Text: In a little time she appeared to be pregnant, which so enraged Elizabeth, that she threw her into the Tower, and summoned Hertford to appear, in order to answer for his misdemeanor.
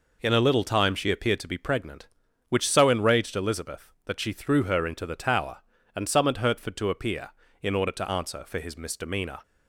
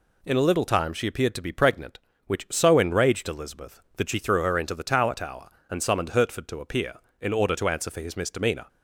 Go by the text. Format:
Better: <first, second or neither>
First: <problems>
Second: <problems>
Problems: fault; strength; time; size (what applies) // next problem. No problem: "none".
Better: first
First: none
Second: says "Tower" twice; at 5.1 s